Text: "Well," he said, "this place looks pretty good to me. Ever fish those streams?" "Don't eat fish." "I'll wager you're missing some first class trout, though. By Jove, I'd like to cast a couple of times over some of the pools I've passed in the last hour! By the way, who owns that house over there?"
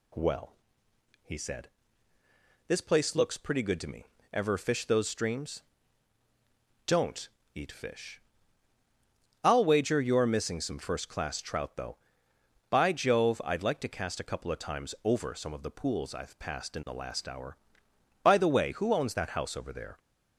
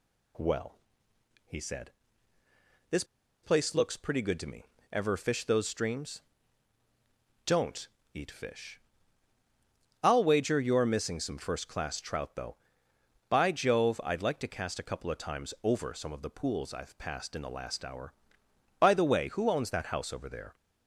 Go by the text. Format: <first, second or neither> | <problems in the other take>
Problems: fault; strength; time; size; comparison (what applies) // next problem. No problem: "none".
first | pauses between "this" and "place"; at 3.0 s; 0.39 s long // pauses between "Don't" and "eat"; slight; at 7.8 s; 0.26 s long; slight in the first